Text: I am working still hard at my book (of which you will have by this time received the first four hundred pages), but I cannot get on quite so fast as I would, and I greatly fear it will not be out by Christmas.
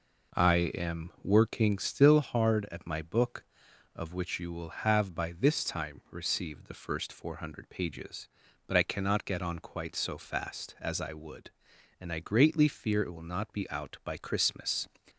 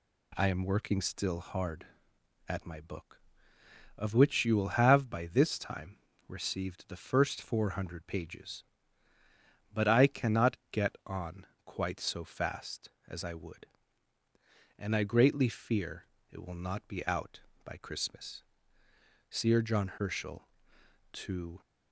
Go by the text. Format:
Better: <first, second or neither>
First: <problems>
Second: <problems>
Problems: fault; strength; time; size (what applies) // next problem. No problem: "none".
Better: first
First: none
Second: pauses between "time" and "received"; slight; at 5.9 s; 0.30 s long // pauses between "on" and "quite"; slight; at 11.4 s; 0.20 s long // pauses between "fear" and "it"; slight; at 16.0 s; 0.26 s long // goes on to say "SIR JOHN HERSCHEL TO"; strong; from 19.2 s on; 2.3 s long